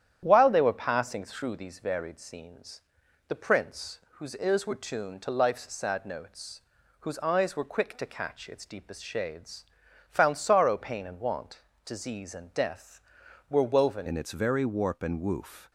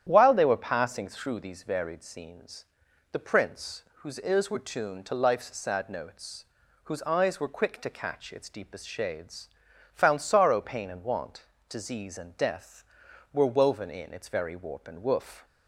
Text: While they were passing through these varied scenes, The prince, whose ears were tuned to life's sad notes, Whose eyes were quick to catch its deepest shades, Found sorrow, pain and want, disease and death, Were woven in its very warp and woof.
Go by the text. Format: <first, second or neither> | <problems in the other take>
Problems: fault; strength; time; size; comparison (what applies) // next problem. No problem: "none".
second | starts louder than the rest; strong; until 1.2 s; 10 dB; strong in the second // changes voice at "in"; from 14.0 s on; 1.7 s long